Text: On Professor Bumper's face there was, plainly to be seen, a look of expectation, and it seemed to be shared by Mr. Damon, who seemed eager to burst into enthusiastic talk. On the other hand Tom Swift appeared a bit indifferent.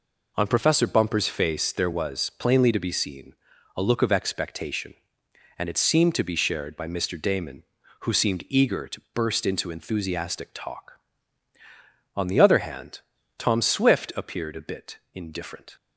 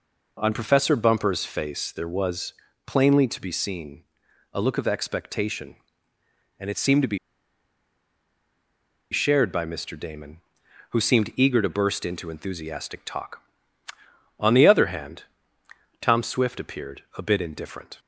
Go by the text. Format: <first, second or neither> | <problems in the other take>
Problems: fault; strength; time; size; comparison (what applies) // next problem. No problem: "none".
first | pauses between "be" and "shared"; strong; at 7.1 s; 1.9 s long // pauses between "hand" and "Tom"; noticeable; at 15.2 s; 0.76 s long; also in the first // pauses between "appeared" and "a"; slight; at 17.0 s; 0.16 s long